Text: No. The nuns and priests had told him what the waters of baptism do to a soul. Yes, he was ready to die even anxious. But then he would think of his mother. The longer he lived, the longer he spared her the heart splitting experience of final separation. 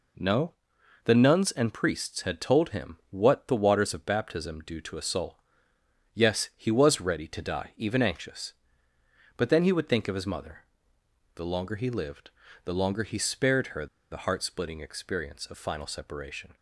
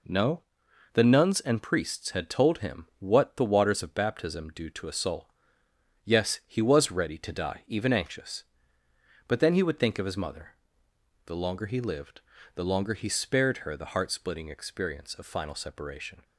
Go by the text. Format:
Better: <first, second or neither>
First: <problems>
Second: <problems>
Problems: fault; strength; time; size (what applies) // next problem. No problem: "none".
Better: second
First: pauses between "her" and "the"; slight; at 13.8 s; 0.25 s long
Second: none